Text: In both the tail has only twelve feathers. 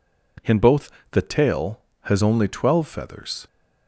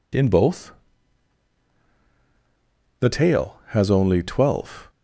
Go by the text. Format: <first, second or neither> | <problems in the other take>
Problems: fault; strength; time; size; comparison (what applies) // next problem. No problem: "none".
first | pauses between "both" and "the"; strong; at 0.6 s; 2.3 s long; slight in the first // stops before "feathers"; at 4.8 s